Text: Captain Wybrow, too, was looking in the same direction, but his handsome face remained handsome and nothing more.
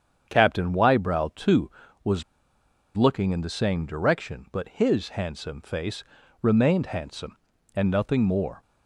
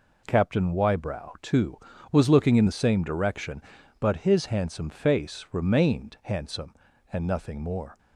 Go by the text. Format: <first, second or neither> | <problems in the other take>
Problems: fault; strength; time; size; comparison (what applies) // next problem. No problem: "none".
second | starts louder than the rest; strong; until 1.3 s; 8 dB // pauses between "was" and "looking"; noticeable; at 2.2 s; 0.74 s long // pauses between "face" and "remained"; at 6.0 s; 0.38 s long